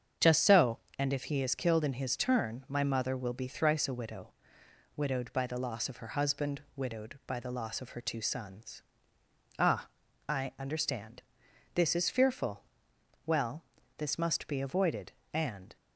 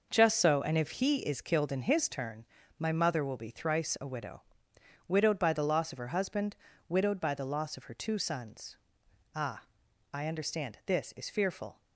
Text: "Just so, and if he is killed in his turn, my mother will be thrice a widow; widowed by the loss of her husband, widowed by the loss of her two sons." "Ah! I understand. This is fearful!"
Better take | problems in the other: second | starts louder than the rest; strong; until 1.4 s; 7.5 dB // goes on to say "Well this must be avoided and"; strong; from 13.2 s on; 2.5 s long

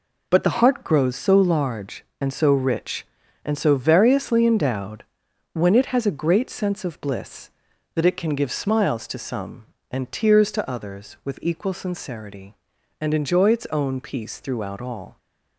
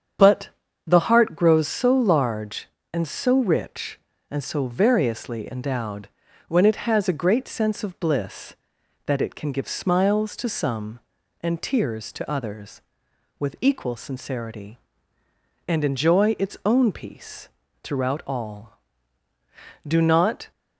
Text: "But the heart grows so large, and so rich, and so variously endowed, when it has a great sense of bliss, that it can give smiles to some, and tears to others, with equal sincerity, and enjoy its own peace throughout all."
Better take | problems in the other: first | starts louder than the rest; strong; until 1.5 s; 8 dB // pauses between "But" and "the"; slight; at 0.5 s; 0.36 s long // pauses between "peace" and "throughout"; slight; at 17.4 s; 0.34 s long // goes on to say "Do not"; noticeable; from 19.8 s on; 0.64 s long

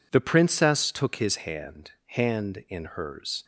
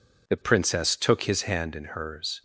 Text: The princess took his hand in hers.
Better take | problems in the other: second | says "hand" twice; at 2.0 s

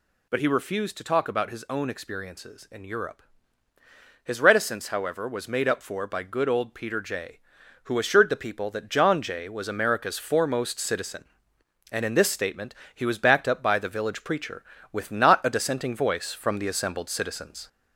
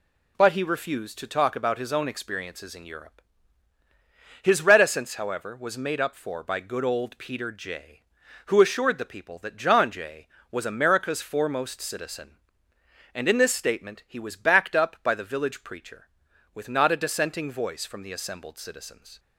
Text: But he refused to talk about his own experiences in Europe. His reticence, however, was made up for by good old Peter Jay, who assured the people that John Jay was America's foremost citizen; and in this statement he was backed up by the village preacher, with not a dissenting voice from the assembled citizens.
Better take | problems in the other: second | gets louder; slight; throughout; 2 dB // pauses between "statement" and "he"; slight; at 12.7 s; 0.18 s long

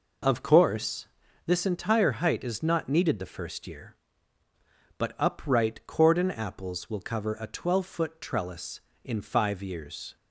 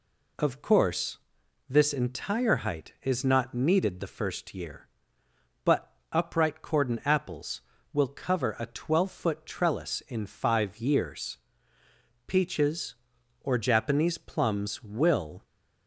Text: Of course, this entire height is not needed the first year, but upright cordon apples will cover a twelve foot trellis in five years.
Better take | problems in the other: first | pauses between "but" and "upright"; slight; at 5.9 s; 0.18 s long // goes on to say "Peaches or Japanese plums will"; strong; from 12.2 s on; 3.1 s long

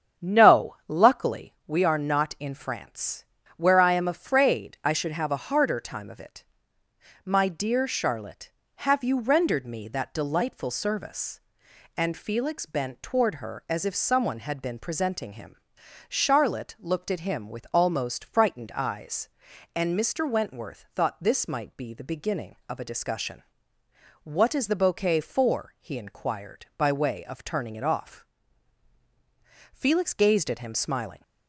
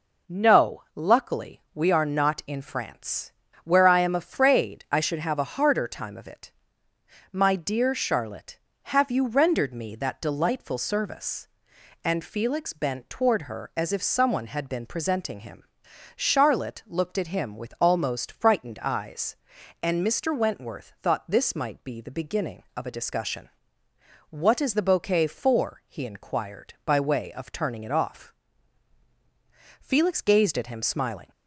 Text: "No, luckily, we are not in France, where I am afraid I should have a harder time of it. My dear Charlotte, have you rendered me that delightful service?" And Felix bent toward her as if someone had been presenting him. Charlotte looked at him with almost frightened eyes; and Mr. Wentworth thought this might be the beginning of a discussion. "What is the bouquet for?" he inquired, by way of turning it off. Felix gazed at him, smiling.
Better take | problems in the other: second | starts louder than the rest; strong; until 1.5 s; 8.5 dB

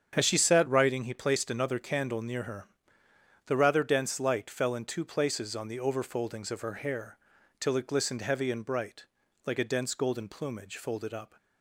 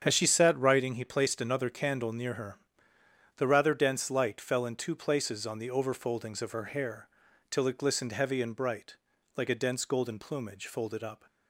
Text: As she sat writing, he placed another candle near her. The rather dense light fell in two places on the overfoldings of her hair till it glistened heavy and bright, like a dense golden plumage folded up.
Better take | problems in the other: neither | starts louder than the rest; strong; the same in both // pauses between "hair" and "till"; the same in both

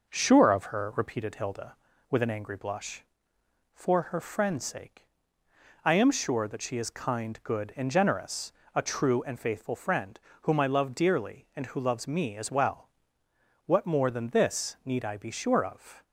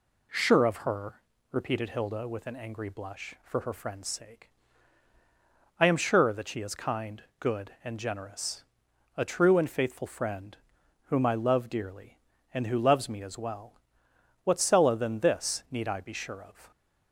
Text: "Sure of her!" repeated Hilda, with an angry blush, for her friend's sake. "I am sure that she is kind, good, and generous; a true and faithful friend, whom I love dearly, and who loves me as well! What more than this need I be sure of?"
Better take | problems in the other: first | says "sella" for "more"; at 14.5 s

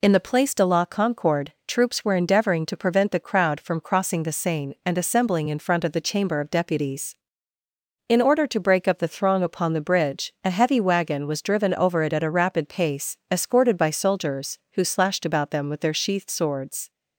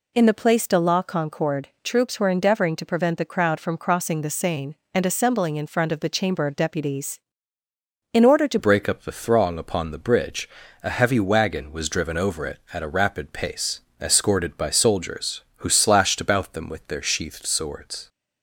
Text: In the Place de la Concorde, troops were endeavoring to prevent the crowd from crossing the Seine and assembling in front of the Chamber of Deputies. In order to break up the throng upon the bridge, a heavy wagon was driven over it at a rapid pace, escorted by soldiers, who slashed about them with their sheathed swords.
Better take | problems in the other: first | changes voice at "break"; from 8.5 s on; 9.5 s long

